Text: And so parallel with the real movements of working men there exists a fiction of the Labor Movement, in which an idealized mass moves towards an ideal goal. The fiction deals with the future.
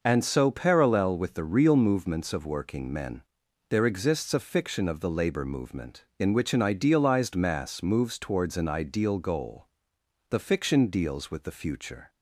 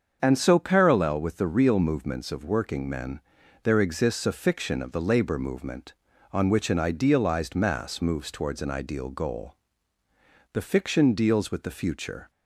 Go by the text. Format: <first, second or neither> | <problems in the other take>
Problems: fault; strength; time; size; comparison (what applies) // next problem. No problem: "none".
first | starts louder than the rest; until 1.2 s; 7 dB // pauses between "men" and "there"; at 3.1 s; 0.44 s long; noticeable in the first // says "on" for "in"; at 6.3 s